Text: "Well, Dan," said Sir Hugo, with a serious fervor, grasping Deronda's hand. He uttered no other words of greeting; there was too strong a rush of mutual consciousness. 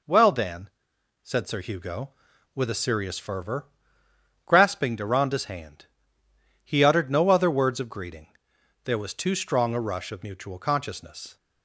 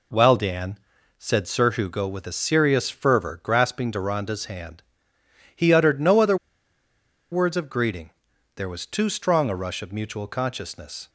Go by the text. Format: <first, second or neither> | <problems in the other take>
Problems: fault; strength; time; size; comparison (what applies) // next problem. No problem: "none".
first | pauses between "other" and "words"; noticeable; at 6.3 s; 0.96 s long